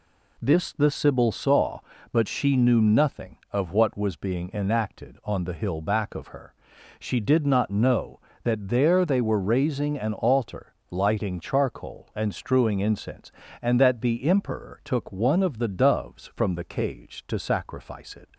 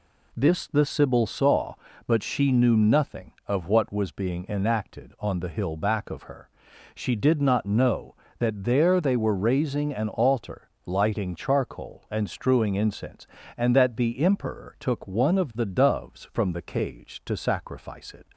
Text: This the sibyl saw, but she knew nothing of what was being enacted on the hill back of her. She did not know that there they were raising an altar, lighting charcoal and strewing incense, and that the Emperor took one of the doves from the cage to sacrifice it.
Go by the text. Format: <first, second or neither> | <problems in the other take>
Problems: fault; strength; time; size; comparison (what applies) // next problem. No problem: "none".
neither | none